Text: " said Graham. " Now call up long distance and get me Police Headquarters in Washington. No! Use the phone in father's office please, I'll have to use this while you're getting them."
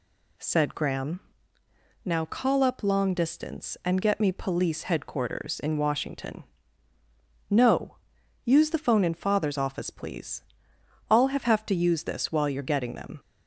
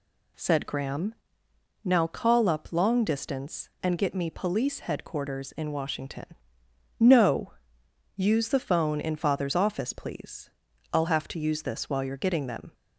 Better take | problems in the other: second | says "have" twice; at 11.4 s

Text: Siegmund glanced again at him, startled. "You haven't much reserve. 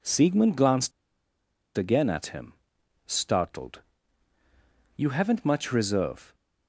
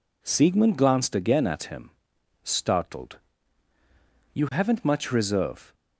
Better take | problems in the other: second | pauses between "glanced" and "again"; noticeable; at 0.9 s; 0.86 s long

